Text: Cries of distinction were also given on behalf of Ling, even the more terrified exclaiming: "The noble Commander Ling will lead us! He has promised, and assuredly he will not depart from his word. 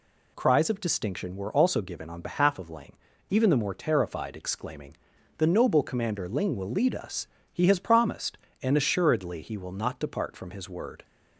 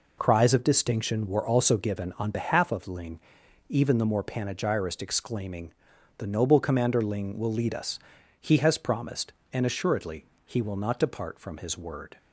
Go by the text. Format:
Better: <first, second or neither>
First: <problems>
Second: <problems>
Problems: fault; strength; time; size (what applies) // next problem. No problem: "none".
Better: first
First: none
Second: says "panegyrist" for "terrified"; at 4.2 s // pauses between "assuredly" and "he"; slight; at 10.2 s; 0.20 s long